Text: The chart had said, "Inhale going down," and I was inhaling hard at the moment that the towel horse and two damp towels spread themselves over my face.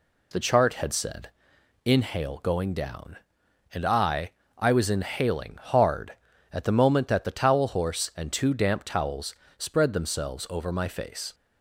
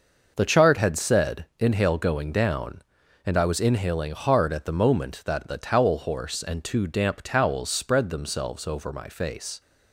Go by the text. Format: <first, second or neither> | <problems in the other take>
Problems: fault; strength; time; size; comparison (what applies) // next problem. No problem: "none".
second | says "I" twice; at 4.5 s // pauses between "towels" and "spread"; slight; at 9.3 s; 0.24 s long